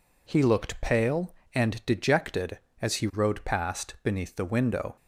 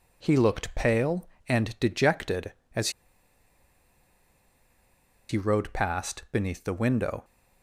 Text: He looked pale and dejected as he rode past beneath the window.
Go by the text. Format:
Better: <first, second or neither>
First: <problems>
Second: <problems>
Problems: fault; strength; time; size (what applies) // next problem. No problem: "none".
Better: first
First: none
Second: pauses between "as" and "he"; strong; at 2.8 s; 2.3 s long